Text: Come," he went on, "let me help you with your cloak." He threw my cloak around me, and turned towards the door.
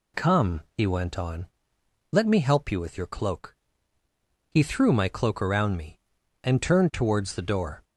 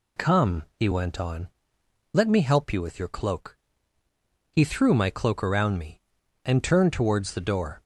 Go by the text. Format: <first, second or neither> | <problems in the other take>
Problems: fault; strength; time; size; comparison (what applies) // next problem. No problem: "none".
neither | none